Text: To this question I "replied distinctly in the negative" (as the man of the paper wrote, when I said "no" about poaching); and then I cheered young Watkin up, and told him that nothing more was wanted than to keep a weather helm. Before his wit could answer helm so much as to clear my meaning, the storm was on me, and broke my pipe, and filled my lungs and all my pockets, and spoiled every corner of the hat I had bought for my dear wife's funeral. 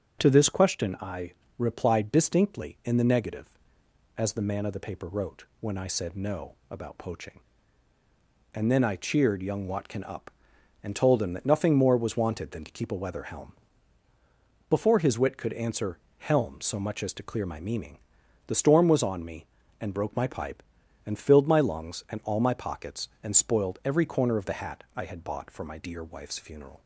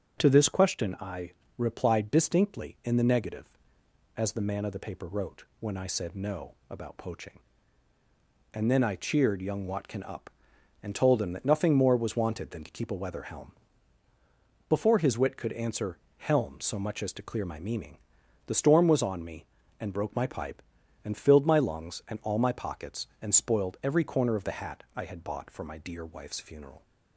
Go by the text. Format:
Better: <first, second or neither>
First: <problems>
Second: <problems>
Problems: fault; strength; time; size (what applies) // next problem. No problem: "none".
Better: neither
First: starts louder than the rest; until 1.2 s; 6.5 dB // pauses between "I" and "replied"; slight; at 1.3 s; 0.26 s long // pauses between "answer" and "helm"; slight; at 15.9 s; 0.18 s long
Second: starts louder than the rest; until 1.2 s; 6.5 dB // pauses between "I" and "replied"; slight; at 1.3 s; 0.26 s long // pauses between "answer" and "helm"; slight; at 15.9 s; 0.18 s long